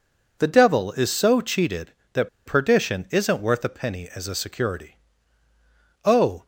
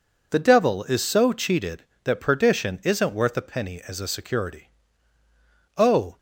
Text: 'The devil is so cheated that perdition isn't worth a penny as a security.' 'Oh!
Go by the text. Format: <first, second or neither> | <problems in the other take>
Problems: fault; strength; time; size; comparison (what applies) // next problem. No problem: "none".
second | pauses between "that" and "perdition"; slight; at 2.2 s; 0.18 s long